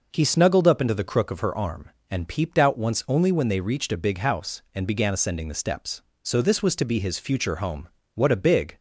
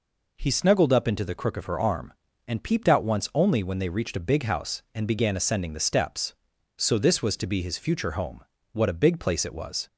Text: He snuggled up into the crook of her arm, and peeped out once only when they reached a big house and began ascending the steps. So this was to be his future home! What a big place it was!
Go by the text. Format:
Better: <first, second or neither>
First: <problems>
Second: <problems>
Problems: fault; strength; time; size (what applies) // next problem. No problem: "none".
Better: second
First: stops before "place it was"; at 8.7 s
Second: none